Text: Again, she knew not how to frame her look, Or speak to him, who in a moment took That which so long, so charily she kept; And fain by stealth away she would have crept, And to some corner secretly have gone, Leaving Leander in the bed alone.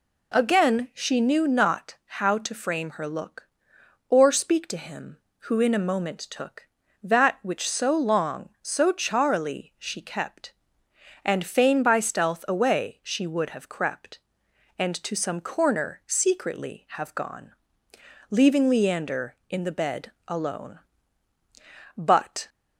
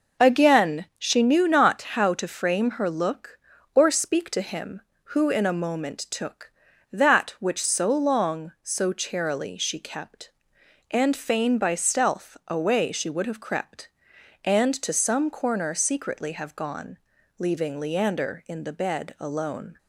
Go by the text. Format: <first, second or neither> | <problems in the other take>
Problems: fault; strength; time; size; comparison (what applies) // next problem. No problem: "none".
second | goes on to say "But"; from 21.9 s on; 0.54 s long